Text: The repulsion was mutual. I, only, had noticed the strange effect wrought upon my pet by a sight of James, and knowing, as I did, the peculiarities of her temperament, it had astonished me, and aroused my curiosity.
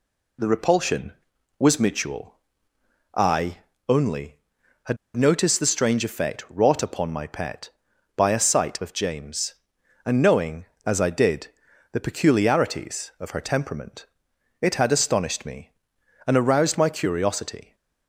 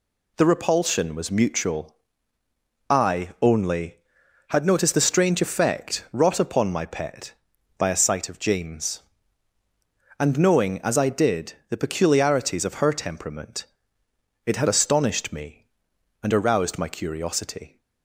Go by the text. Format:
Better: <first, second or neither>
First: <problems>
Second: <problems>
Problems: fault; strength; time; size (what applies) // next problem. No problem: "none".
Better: second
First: pauses between "had" and "noticed"; slight; at 4.9 s; 0.18 s long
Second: none